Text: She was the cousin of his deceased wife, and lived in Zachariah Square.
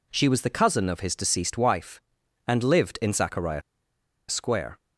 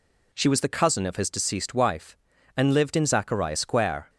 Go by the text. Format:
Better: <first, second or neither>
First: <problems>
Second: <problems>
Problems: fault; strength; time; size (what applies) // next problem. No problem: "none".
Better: second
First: pauses between "Zachariah" and "Square"; noticeable; at 3.6 s; 0.69 s long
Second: none